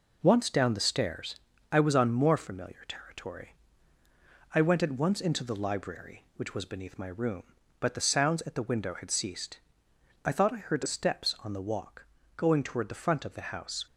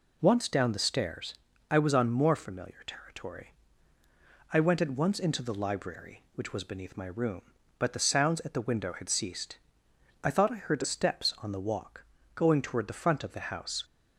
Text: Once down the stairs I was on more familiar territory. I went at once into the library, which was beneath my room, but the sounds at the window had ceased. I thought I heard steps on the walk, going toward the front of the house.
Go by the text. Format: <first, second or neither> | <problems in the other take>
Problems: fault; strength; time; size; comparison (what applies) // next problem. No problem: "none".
second | gets quieter; noticeable; throughout; 5.5 dB // pauses between "stairs" and "I"; slight; at 1.3 s; 0.36 s long; slight in the second